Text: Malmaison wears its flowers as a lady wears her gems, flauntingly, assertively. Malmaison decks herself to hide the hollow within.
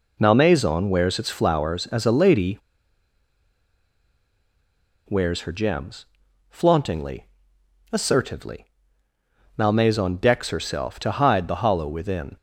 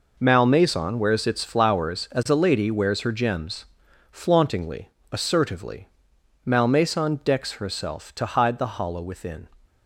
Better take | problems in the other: second | pauses between "lady" and "wears"; strong; at 2.5 s; 2.5 s long

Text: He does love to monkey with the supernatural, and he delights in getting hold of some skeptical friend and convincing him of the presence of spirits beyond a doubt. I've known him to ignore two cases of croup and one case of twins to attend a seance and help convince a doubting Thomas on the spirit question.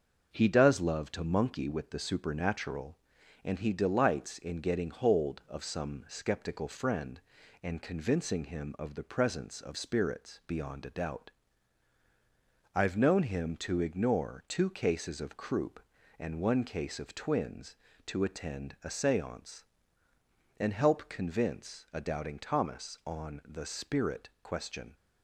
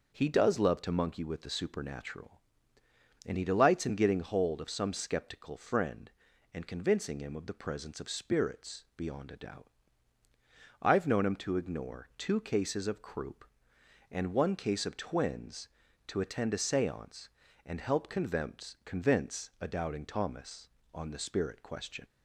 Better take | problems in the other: first | says "convince" twice; at 18.8 s

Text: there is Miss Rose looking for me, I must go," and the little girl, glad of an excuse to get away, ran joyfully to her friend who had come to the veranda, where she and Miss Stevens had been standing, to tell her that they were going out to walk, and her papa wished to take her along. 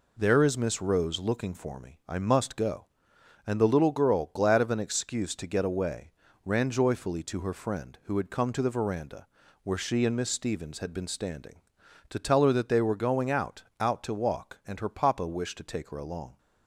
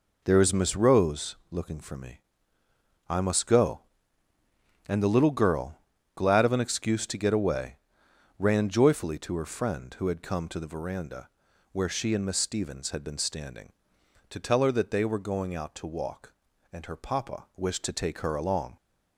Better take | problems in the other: second | says "out" twice; at 13.7 s

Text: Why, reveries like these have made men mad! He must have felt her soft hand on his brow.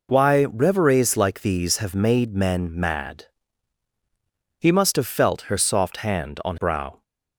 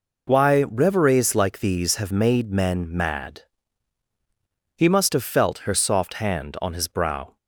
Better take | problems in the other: second | skips "his"; at 6.5 s

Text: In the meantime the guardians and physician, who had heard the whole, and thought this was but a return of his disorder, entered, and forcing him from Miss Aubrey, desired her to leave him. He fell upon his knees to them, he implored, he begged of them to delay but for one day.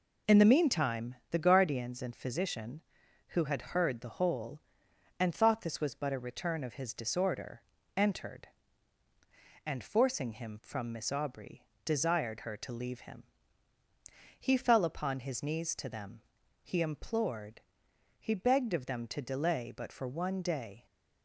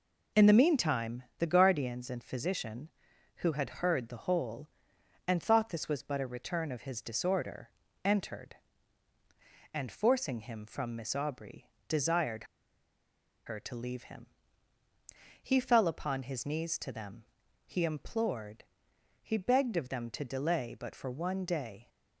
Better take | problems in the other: first | pauses between "meantime" and "the"; slight; at 1.2 s; 0.16 s long; slight in the first // pauses between "desired" and "her"; at 12.4 s; 1.0 s long

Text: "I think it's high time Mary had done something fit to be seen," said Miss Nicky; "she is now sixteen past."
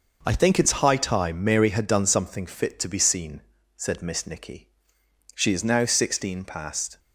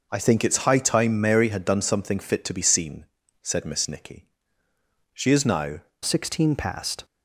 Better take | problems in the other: first | changes voice at "sixteen"; from 6.0 s on; 1.0 s long

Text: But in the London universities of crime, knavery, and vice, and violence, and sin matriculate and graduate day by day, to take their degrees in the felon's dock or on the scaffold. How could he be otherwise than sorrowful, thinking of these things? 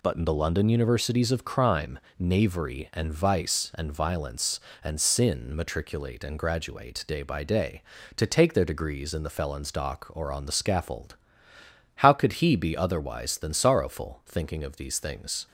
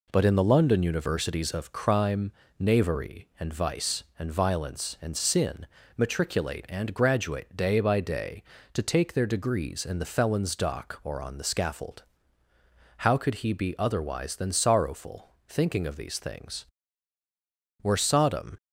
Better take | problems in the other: first | pauses between "sin" and "matriculate"; slight; at 5.6 s; 0.32 s long // goes on to say "Were Sodom"; noticeable; from 17.8 s on; 0.76 s long

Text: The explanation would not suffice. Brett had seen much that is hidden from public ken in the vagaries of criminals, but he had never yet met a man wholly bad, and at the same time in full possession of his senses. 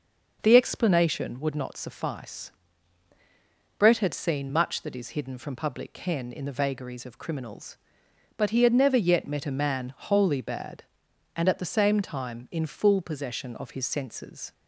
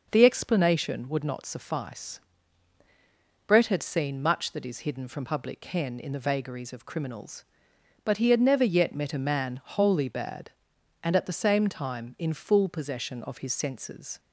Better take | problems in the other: neither | none

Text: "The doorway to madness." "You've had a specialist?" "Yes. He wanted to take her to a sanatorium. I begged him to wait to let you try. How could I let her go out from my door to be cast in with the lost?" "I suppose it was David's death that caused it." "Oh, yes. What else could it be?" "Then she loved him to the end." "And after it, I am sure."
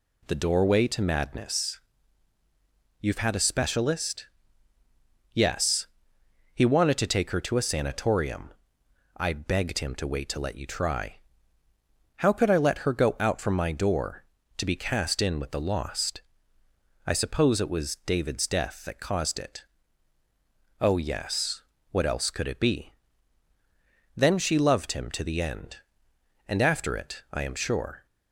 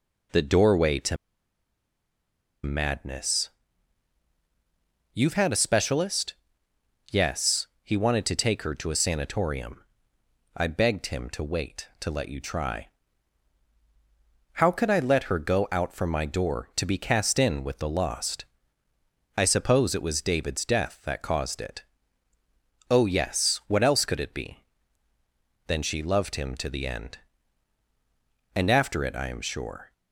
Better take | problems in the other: first | pauses between "to" and "madness"; strong; at 1.1 s; 1.4 s long

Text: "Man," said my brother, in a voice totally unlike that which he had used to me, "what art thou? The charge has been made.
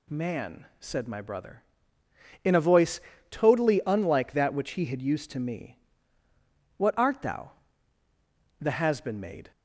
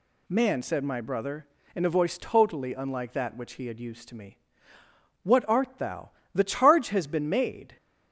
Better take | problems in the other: second | pauses between "voice" and "totally"; slight; at 2.9 s; 0.30 s long // skips "charge"; at 8.7 s

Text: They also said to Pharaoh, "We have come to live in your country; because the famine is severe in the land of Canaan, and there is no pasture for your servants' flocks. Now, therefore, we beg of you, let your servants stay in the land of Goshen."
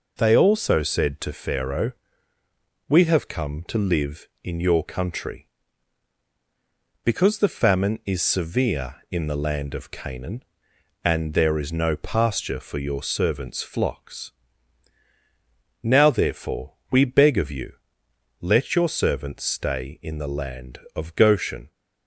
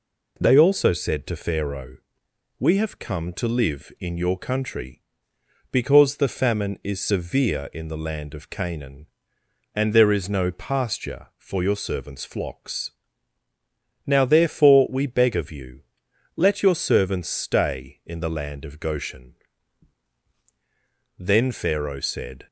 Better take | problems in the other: first | goes on to say "Then Pharaoh said"; noticeable; from 21.1 s on; 1.3 s long

